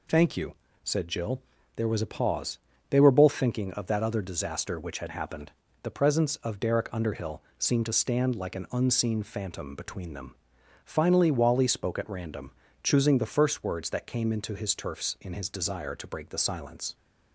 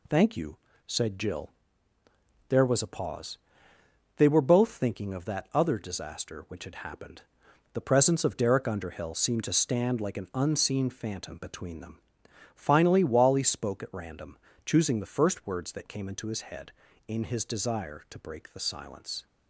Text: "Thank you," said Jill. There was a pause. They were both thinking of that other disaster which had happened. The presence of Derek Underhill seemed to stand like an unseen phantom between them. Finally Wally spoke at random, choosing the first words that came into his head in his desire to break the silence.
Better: second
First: pauses between "Underhill" and "seemed"; slight; at 7.4 s; 0.18 s long // says "turfs" for "head"; at 14.7 s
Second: none

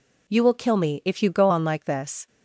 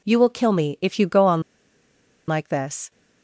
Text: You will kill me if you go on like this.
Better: first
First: none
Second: pauses between "on" and "like"; noticeable; at 1.4 s; 0.85 s long

